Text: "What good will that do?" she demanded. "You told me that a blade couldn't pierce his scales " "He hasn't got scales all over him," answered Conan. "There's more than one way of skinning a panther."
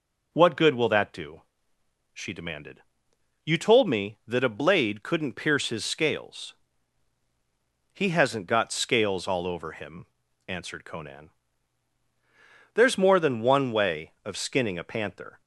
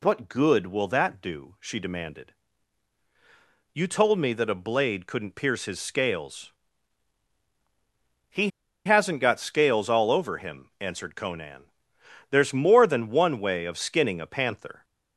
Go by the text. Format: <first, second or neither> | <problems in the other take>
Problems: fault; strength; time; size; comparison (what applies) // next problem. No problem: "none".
first | pauses between "He" and "hasn't"; at 8.4 s; 0.36 s long